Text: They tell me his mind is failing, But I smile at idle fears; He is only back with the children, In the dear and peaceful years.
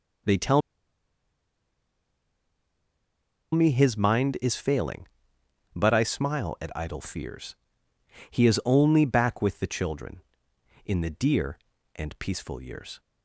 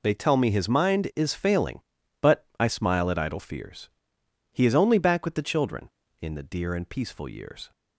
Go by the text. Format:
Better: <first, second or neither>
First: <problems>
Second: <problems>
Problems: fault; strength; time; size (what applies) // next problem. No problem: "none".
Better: second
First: pauses between "tell" and "me"; strong; at 0.6 s; 2.9 s long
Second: none